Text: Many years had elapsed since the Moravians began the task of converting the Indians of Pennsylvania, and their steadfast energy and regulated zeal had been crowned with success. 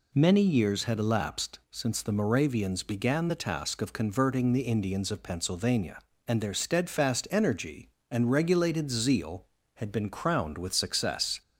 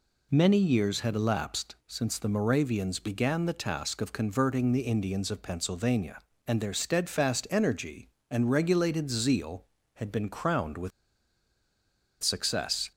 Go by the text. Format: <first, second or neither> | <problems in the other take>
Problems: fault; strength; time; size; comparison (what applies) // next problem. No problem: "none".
first | pauses between "with" and "success"; strong; at 10.9 s; 1.3 s long